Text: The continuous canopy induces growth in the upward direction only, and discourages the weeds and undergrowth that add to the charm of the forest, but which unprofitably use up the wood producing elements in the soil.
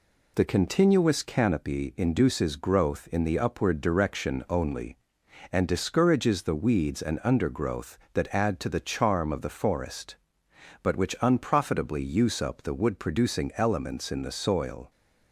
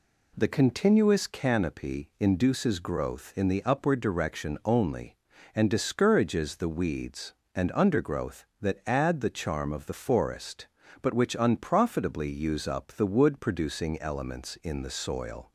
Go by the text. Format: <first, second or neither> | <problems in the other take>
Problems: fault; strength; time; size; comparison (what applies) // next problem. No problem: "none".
first | skips "to"; at 9.2 s